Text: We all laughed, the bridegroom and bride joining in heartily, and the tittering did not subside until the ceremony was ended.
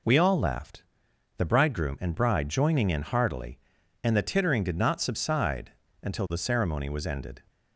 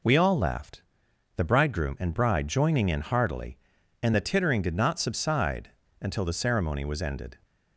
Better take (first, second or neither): neither